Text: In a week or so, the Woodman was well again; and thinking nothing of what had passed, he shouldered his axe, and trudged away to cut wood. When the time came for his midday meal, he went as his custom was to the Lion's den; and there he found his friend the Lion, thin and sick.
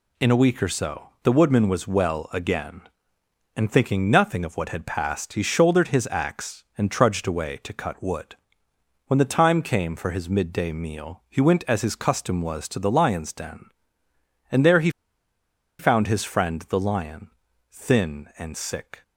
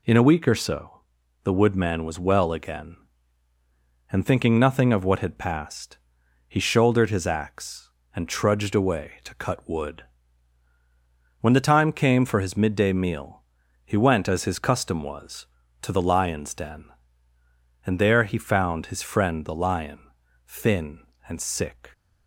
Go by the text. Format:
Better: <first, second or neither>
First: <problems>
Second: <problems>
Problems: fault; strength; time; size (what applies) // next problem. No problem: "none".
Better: second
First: pauses between "he" and "found"; noticeable; at 14.8 s; 0.89 s long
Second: none